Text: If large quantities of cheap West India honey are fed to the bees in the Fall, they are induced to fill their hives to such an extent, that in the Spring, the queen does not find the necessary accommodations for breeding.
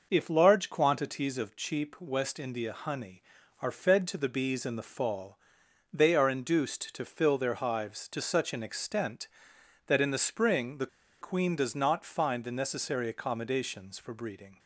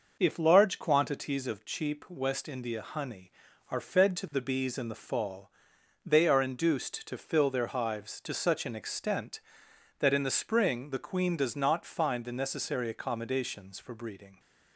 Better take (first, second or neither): second